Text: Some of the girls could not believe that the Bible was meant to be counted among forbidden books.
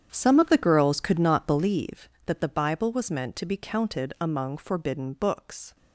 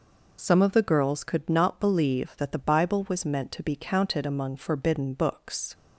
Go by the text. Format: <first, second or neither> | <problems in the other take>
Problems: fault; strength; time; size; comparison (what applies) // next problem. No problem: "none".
second | starts louder than the rest; strong; until 1.8 s; 8.5 dB